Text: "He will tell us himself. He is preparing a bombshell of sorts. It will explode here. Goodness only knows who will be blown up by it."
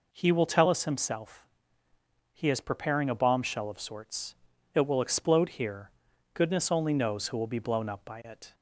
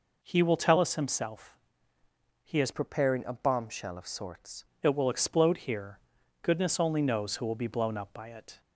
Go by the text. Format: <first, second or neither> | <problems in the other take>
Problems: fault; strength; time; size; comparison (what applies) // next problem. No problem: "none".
first | changes voice from "preparing" to "sorts"; from 2.7 to 4.6 s; 1.9 s long